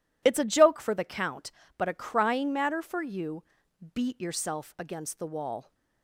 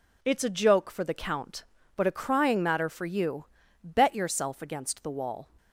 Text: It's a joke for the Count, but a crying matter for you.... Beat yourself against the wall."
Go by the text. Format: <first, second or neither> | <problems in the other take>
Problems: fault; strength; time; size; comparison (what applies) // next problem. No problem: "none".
first | says "Bet" for "Beat"; at 3.8 s